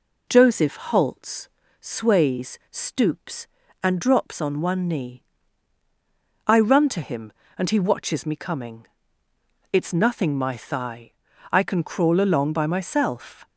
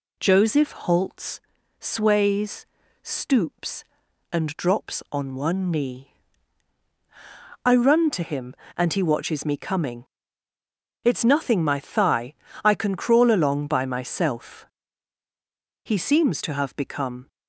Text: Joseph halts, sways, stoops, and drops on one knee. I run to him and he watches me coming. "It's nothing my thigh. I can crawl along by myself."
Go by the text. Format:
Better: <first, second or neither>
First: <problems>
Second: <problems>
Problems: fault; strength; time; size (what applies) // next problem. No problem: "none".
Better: first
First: none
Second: goes on to say "He seems to have become"; from 15.8 s on; 1.4 s long